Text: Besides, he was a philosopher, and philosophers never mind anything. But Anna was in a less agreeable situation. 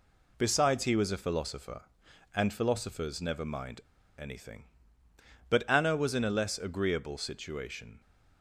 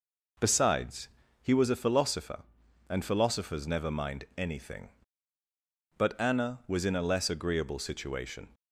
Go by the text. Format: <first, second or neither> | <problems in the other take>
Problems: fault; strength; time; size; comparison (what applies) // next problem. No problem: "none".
second | pauses between "mind" and "anything"; at 3.8 s; 0.37 s long